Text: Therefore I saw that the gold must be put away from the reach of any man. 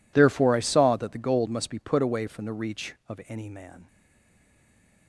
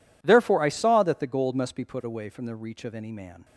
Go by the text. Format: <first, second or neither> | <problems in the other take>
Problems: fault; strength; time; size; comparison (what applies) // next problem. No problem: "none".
second | stays silent after the last word; noticeable; from 3.8 s on; 1.2 s long